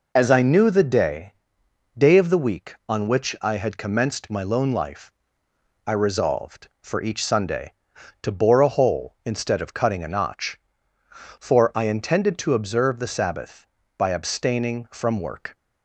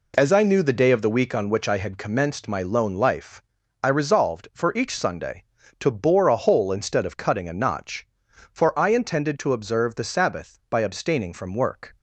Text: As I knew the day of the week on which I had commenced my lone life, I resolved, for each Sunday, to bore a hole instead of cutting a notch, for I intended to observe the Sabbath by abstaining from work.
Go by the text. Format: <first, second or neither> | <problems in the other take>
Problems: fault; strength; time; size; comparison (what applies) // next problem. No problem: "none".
second | says "day" twice; at 1.9 s